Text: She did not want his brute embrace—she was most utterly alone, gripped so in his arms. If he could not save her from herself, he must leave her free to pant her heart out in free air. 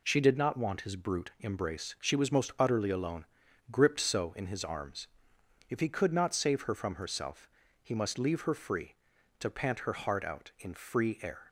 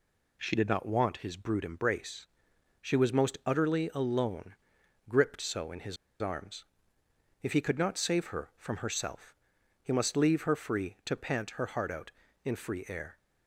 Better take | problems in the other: first | pauses between "his" and "arms"; slight; at 5.9 s; 0.25 s long

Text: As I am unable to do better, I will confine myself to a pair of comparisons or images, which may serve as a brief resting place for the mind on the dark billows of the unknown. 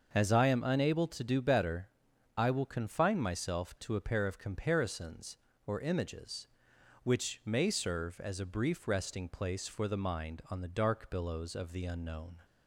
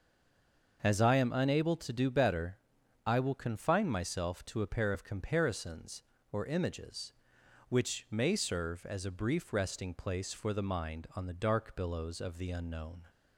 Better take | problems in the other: first | stays silent before the first word; slight; until 0.8 s; 0.8 s long // starts louder than the rest; until 1.8 s; 6.5 dB; also in the first

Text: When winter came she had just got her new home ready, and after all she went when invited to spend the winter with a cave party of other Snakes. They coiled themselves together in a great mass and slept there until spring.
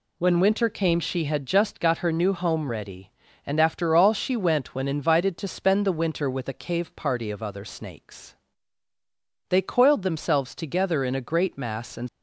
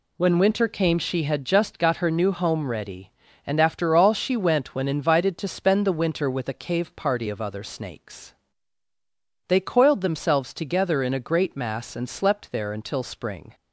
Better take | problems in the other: second | stops before "slept there until spring"; at 12.0 s

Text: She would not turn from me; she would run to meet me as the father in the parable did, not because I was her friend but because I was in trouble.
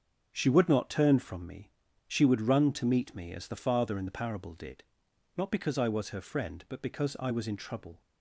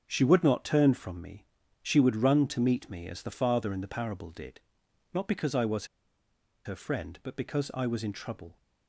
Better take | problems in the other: first | starts louder than the rest; until 1.0 s; 7 dB; also in the first // pauses between "was" and "her"; noticeable; at 5.8 s; 0.80 s long

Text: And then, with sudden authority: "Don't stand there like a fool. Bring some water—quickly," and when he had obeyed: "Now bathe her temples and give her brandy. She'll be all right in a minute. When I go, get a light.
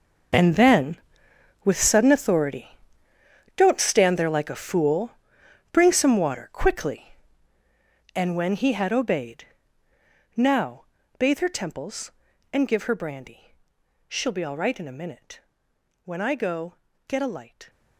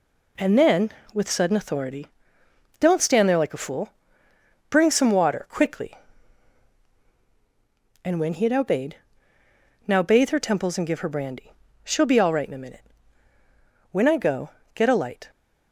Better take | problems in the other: second | gets quieter; strong; throughout; 16 dB // pauses between "Now" and "bathe"; slight; at 10.8 s; 0.34 s long

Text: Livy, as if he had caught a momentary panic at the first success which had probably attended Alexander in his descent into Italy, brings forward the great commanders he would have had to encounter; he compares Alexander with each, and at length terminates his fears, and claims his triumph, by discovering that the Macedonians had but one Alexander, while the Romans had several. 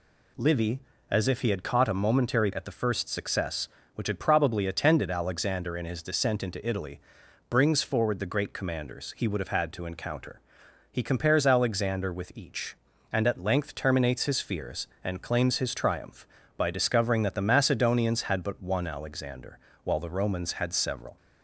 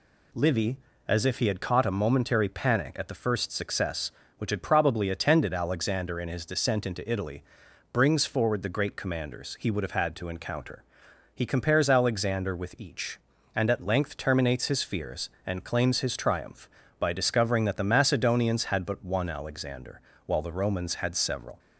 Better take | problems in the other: second | skips "panic"; at 2.5 s

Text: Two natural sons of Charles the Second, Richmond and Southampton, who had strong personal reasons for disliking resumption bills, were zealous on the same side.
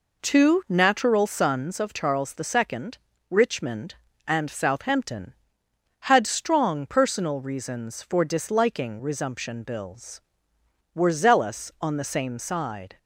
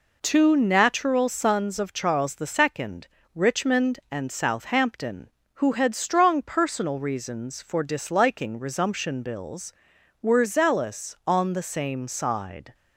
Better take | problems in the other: second | skips "who"; at 5.6 s

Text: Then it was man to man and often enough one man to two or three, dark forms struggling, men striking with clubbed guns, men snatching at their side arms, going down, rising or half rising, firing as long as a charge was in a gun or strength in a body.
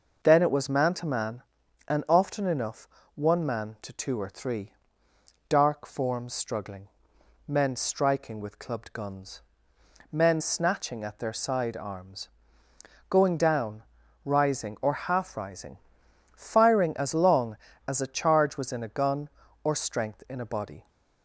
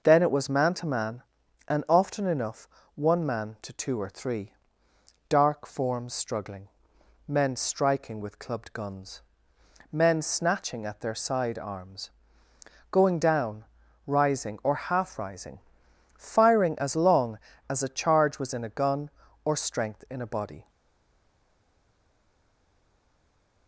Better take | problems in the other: first | pauses between "enough" and "one"; slight; at 2.6 s; 0.26 s long; slight in the first // stays silent after the last word; strong; from 20.6 s on; 3.0 s long

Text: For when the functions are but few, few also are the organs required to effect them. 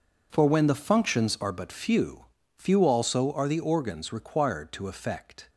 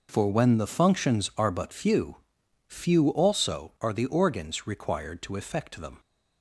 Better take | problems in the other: second | stops before "them"; at 5.4 s

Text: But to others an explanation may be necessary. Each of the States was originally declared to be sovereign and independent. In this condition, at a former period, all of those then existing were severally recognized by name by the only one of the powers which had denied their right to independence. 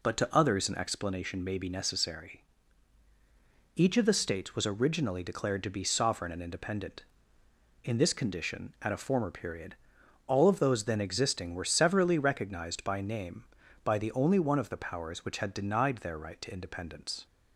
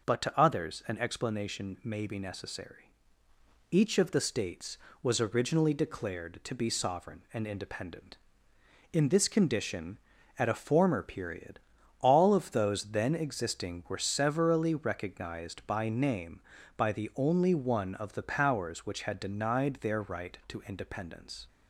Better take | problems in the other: neither | none

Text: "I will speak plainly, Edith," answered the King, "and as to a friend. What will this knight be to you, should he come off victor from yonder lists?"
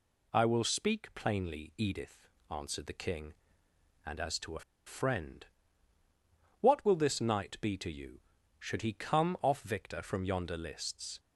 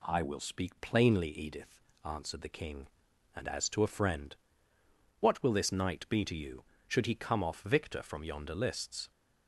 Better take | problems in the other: second | pauses between "a" and "friend"; slight; at 4.6 s; 0.25 s long

